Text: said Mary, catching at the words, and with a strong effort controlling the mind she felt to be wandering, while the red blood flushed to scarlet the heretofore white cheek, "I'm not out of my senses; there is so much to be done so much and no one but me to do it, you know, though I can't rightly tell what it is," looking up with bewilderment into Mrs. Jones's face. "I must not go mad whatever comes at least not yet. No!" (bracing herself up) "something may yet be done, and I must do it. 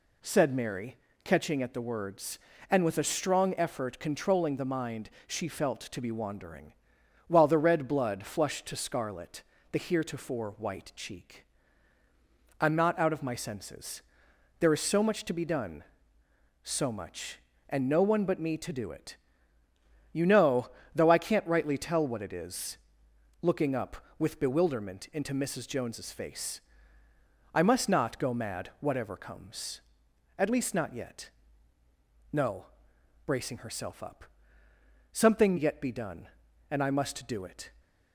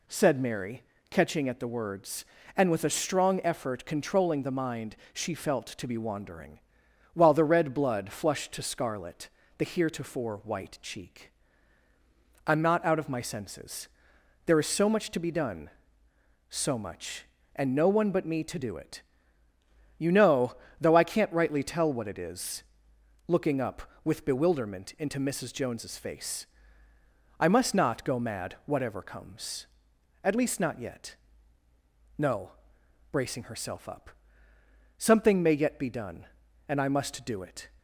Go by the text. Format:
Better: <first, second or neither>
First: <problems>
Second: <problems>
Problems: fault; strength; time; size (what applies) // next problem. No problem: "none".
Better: second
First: pauses between "mind" and "she"; slight; at 5.0 s; 0.16 s long // pauses between "scarlet" and "the"; slight; at 9.4 s; 0.30 s long // skips "may"; at 35.5 s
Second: pauses between "mind" and "she"; slight; at 4.9 s; 0.16 s long // pauses between "scarlet" and "the"; slight; at 9.2 s; 0.30 s long